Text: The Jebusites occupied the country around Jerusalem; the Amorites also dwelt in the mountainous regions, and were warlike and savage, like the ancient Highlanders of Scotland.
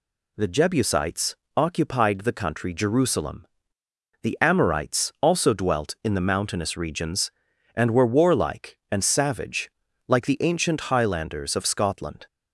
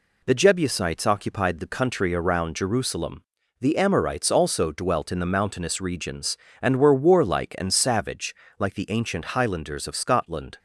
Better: second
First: pauses between "Jebusites" and "occupied"; slight; at 1.3 s; 0.20 s long // skips "around"; at 2.7 s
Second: none

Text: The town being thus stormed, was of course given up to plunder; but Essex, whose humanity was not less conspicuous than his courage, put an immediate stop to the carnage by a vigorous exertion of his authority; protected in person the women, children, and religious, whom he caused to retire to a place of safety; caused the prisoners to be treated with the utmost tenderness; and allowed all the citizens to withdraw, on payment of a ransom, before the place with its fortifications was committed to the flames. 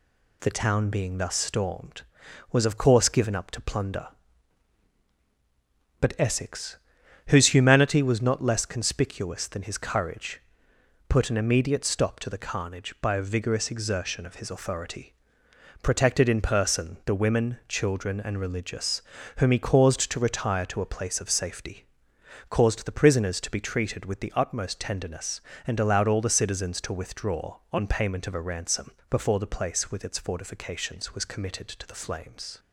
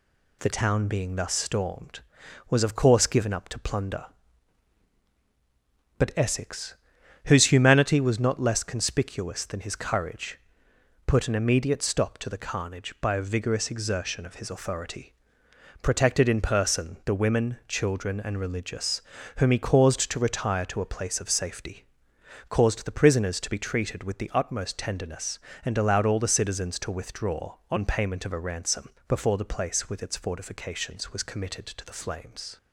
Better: neither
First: none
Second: none

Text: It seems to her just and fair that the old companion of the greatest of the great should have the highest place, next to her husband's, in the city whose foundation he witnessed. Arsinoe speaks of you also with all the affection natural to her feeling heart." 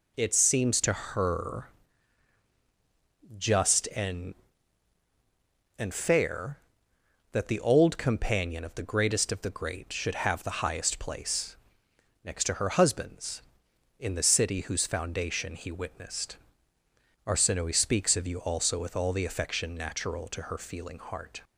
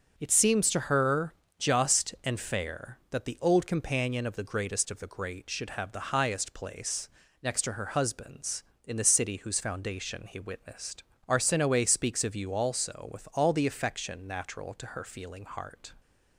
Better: second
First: pauses between "her" and "just"; strong; at 1.6 s; 1.7 s long // says "and" twice; at 5.7 s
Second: pauses between "her" and "just"; slight; at 1.3 s; 0.24 s long

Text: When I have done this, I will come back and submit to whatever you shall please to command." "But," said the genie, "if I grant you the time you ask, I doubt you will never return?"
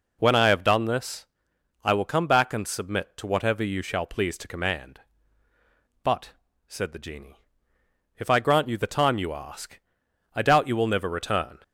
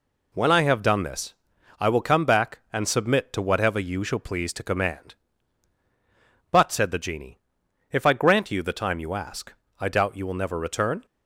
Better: neither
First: none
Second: none

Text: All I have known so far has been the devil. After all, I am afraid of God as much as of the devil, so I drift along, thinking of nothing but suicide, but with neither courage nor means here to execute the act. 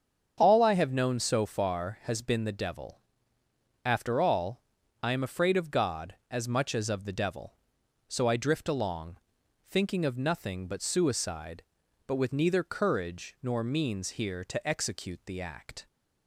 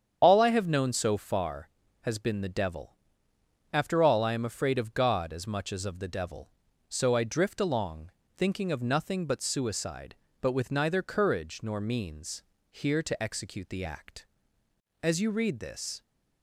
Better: first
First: starts louder than the rest; strong; until 1.3 s; 7.5 dB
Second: starts louder than the rest; strong; until 1.2 s; 8 dB // pauses between "means" and "here"; slight; at 12.4 s; 0.29 s long // goes on to say "As you read this"; noticeable; from 15.0 s on; 1.0 s long

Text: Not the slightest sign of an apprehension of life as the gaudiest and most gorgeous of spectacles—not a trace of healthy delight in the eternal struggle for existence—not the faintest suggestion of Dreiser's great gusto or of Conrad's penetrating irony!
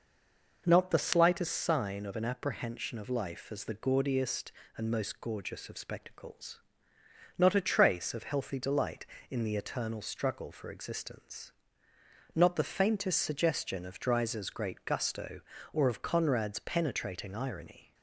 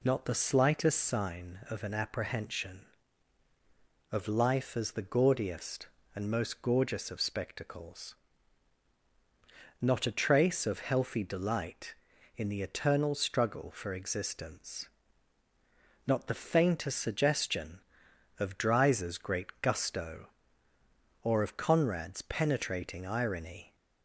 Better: second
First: stays silent before the first word; slight; until 0.6 s; 0.6 s long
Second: none

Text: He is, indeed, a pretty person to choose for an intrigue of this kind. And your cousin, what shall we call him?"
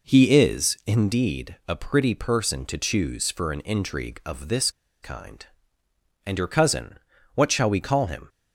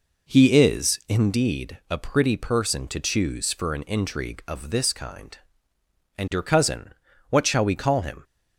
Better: second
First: pauses between "this" and "kind"; slight; at 4.7 s; 0.32 s long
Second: none

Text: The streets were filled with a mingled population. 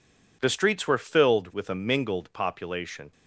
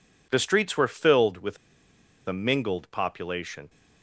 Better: first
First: none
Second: pauses between "with" and "a"; noticeable; at 1.5 s; 0.70 s long

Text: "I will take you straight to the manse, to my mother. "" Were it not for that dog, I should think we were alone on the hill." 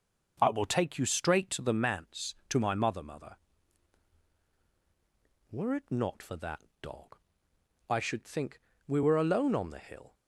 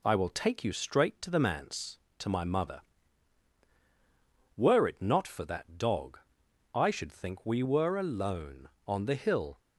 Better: second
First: starts louder than the rest; strong; until 1.4 s; 7.5 dB // says "mother" twice; at 3.0 s // pauses between "that" and "dog"; slight; at 6.6 s; 0.18 s long // pauses between "think" and "we"; slight; at 8.6 s; 0.26 s long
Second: none

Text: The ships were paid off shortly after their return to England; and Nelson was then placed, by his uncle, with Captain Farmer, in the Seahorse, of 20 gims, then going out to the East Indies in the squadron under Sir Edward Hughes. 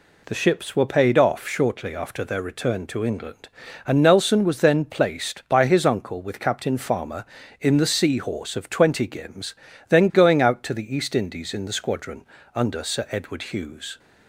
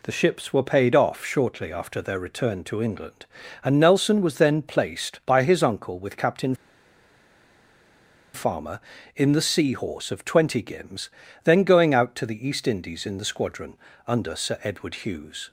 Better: first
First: pauses between "squadron" and "under"; slight; at 12.2 s; 0.32 s long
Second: pauses between "Captain" and "Farmer"; strong; at 6.5 s; 1.7 s long // pauses between "squadron" and "under"; slight; at 13.7 s; 0.32 s long

